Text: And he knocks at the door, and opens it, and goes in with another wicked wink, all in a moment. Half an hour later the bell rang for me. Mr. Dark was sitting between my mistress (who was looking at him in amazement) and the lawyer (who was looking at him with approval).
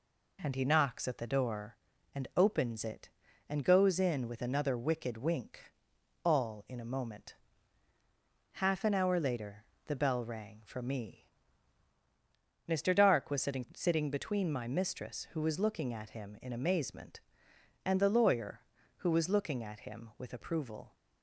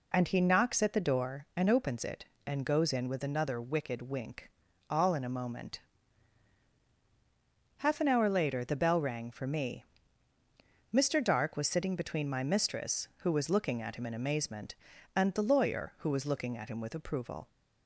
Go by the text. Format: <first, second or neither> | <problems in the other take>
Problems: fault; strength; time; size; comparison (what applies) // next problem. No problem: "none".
second | pauses between "later" and "the"; slight; at 9.6 s; 0.22 s long // says "sitting" twice; at 13.7 s